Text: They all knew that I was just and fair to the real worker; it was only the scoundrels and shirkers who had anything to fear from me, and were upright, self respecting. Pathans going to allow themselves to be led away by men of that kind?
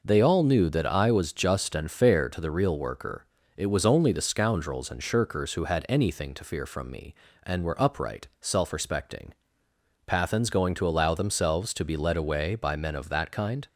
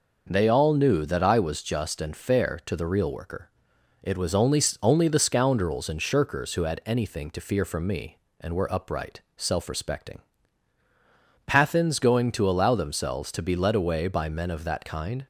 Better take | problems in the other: first | says "only" twice; at 4.8 s

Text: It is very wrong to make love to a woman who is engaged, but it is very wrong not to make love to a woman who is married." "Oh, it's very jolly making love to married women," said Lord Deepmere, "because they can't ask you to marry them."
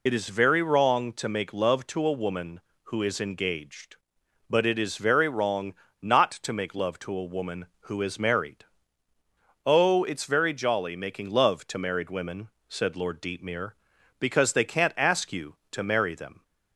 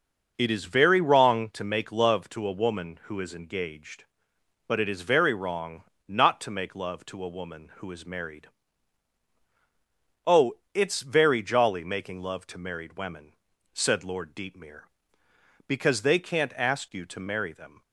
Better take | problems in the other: second | loses the start of "It"; at 0.0 s; 25 ms // pauses between "wrong" and "not"; slight; at 5.7 s; 0.27 s long; slight in the second

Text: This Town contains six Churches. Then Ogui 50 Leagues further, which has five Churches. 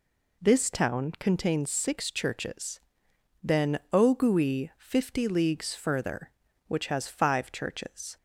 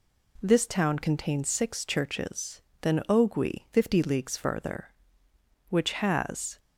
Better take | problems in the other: first | stops before "five Churches"; at 6.5 s

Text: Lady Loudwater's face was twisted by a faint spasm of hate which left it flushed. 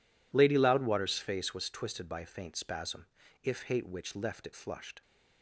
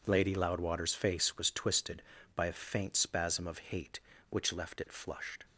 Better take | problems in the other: second | says "if" for "of"; at 3.4 s

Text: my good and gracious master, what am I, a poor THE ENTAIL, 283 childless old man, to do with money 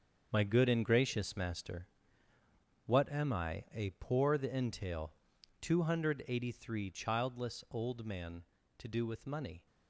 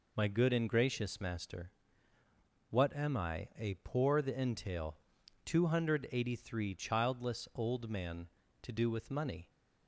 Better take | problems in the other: second | gets quieter; strong; throughout; 10 dB

